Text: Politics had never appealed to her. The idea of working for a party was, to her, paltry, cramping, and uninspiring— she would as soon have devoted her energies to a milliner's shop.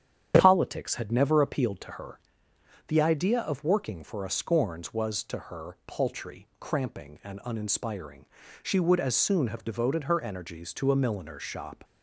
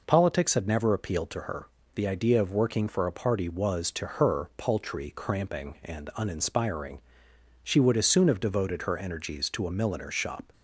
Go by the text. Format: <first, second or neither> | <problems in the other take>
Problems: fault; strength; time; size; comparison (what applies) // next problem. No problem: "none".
second | starts louder than the rest; strong; until 1.4 s; 8.5 dB // says "scorns" for "party"; at 4.2 s